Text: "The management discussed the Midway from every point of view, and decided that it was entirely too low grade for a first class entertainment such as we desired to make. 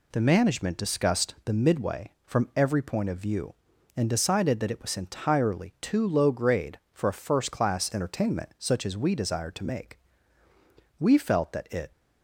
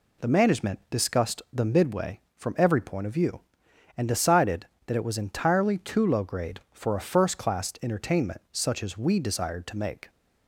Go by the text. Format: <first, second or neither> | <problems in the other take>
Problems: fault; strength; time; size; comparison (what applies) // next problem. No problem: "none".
second | goes on to say "We felt that it"; noticeable; from 10.9 s on; 0.92 s long